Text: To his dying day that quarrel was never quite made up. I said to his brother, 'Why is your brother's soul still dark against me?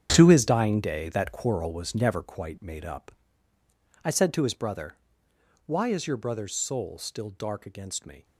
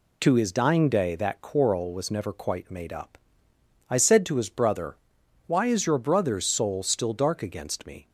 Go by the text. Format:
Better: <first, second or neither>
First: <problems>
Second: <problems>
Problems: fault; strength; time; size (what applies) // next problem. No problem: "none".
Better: second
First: gets quieter; strong; throughout; 11.5 dB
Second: none